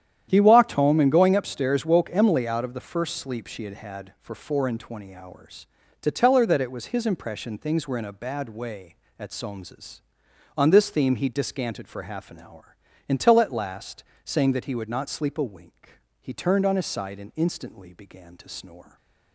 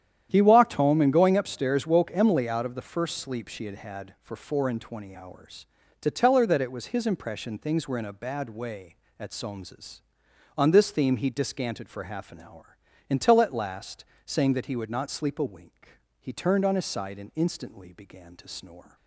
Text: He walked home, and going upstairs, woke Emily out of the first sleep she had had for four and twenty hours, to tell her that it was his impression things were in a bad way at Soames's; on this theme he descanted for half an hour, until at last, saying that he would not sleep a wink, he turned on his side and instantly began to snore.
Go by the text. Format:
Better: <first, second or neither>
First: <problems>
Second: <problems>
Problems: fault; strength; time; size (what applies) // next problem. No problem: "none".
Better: neither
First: starts louder than the rest; strong; until 1.3 s; 10 dB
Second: starts louder than the rest; strong; until 1.3 s; 10 dB